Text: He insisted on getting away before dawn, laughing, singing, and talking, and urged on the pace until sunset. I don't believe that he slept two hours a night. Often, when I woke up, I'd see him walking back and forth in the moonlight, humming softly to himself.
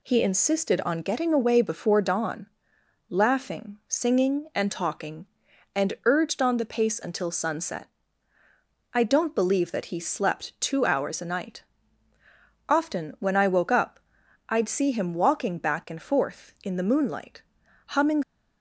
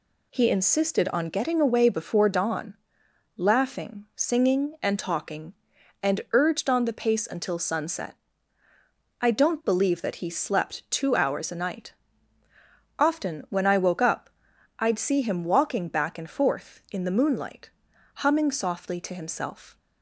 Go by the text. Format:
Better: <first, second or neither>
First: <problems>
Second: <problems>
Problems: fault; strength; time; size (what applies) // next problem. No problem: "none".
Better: second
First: stops before "softly to himself"; at 18.2 s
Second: none